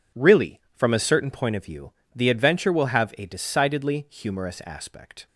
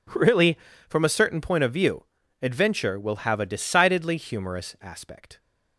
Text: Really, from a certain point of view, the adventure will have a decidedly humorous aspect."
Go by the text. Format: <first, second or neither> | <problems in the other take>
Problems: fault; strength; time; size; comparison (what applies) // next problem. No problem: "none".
first | skips "the"; at 2.2 s